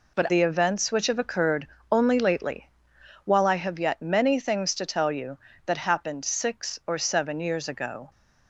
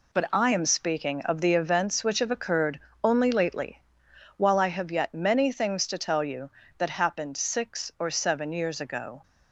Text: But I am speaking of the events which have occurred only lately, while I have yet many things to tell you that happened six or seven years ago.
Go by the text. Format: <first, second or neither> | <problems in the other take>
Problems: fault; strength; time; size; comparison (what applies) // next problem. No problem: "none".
second | skips "I am speaking of"; at 0.2 s // pauses between "occurred" and "only"; slight; at 1.6 s; 0.20 s long; slight in the second